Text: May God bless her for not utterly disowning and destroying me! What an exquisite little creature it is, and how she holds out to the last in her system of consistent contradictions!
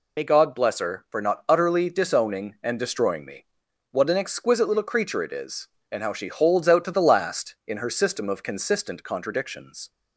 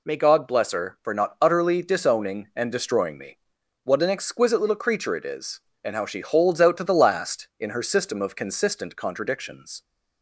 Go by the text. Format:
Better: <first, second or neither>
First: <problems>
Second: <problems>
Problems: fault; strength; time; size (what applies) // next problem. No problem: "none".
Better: second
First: loses the start of "May"; at 0.1 s; 40 ms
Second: none